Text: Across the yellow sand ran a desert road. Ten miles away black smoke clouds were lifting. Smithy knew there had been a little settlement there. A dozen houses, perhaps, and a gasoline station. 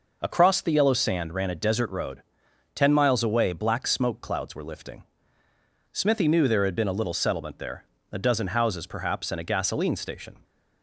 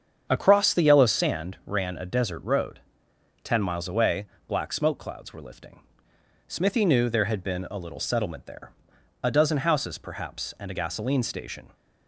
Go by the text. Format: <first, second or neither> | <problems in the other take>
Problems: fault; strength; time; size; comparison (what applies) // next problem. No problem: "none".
first | starts louder than the rest; strong; until 1.3 s; 7.5 dB // pauses between "away" and "black"; slight; at 4.2 s; 0.24 s long